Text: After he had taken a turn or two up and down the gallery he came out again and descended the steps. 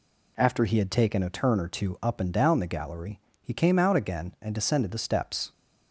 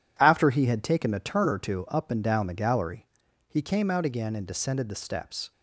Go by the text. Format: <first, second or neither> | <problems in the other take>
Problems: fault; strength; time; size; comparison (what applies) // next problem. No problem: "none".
first | gets quieter; strong; throughout; 9 dB // pauses between "gallery" and "he"; at 3.0 s; 0.44 s long; slight in the first